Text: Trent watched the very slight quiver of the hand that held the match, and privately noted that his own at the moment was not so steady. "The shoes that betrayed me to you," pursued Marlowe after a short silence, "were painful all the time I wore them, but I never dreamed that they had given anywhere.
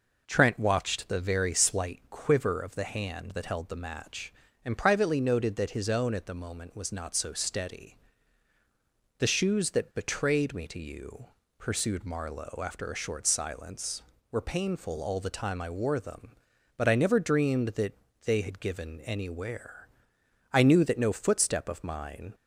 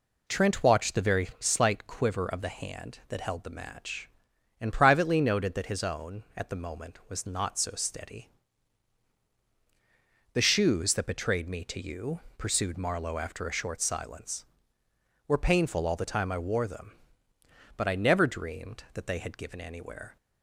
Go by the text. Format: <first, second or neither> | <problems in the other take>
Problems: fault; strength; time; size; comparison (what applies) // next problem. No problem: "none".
second | pauses between "that" and "they"; slight; at 17.9 s; 0.28 s long // goes on to say "I knew that no footstep of mine"; strong; from 20.5 s on; 1.8 s long